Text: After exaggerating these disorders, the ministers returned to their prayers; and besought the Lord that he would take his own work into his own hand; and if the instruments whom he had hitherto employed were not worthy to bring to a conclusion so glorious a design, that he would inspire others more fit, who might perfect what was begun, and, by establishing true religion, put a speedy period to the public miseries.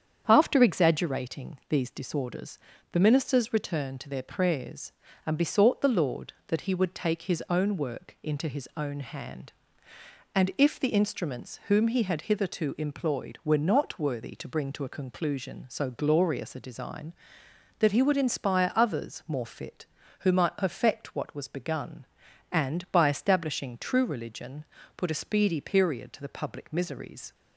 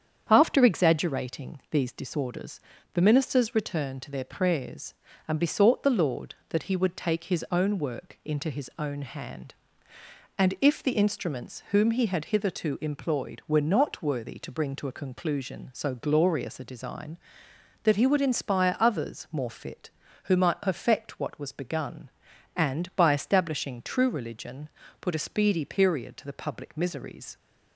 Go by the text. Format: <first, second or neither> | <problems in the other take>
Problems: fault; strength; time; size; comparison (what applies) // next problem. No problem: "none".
neither | starts louder than the rest; strong; the same in both